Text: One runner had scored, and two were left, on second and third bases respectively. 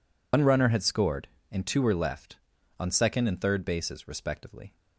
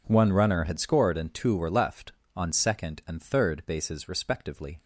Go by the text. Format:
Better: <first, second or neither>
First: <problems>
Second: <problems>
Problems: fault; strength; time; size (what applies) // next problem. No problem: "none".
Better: second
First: loses the start of "One"; at 0.3 s; 80 ms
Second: none